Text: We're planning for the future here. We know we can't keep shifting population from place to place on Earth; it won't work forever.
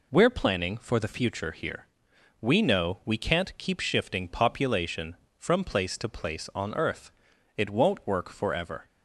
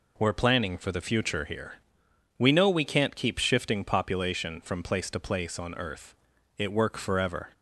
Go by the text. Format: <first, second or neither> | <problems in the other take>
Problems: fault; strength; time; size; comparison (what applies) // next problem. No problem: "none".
first | skips "won't"; at 6.7 s